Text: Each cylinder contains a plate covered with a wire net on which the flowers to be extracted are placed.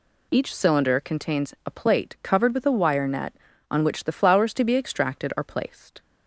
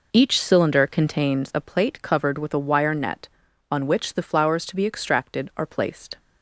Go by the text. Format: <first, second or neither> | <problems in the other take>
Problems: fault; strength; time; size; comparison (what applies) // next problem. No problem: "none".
first | starts louder than the rest; noticeable; until 1.4 s; 4.5 dB